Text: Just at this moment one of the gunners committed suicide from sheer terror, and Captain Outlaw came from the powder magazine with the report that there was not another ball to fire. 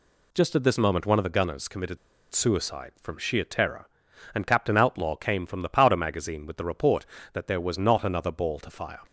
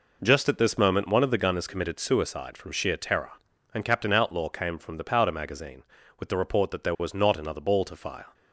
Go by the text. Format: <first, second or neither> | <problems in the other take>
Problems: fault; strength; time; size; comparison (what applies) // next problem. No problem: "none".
second | pauses between "committed" and "suicide"; at 1.9 s; 0.36 s long